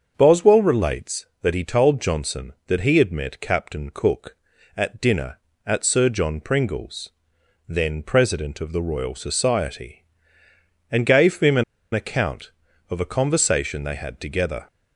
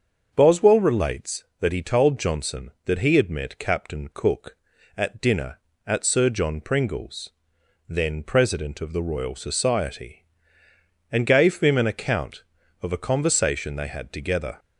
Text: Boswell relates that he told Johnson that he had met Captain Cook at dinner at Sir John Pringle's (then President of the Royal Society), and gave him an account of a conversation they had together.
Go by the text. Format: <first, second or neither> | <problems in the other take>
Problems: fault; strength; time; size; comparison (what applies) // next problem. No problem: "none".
second | starts louder than the rest; until 1.1 s; 6.5 dB; also in the second // pauses between "an" and "account"; slight; at 11.6 s; 0.30 s long